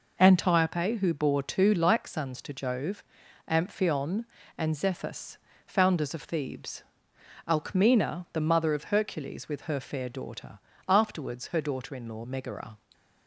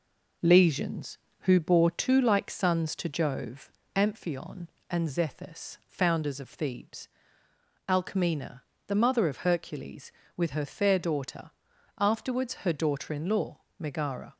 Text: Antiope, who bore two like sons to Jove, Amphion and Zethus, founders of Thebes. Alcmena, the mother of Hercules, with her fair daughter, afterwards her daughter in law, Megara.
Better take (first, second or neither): first